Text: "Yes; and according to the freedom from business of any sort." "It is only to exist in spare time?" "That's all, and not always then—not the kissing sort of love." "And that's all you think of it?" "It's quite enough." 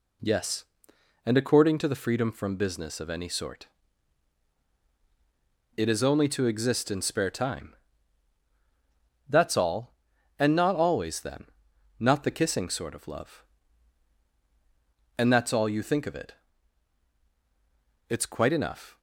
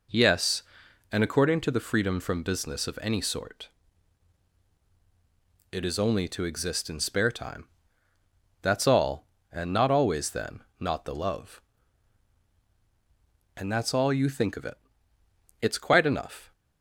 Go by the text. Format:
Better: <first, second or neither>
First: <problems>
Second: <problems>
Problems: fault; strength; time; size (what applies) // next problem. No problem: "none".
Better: first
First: none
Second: skips "kissing sort of"; at 11.1 s